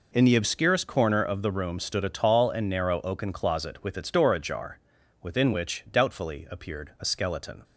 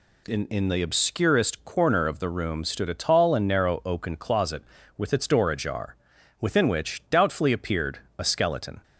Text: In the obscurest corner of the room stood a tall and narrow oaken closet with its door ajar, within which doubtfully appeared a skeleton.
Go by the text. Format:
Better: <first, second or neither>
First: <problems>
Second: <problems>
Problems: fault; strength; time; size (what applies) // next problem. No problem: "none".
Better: first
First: none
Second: says "In" twice; at 0.4 s // pauses between "appeared" and "a"; slight; at 7.9 s; 0.18 s long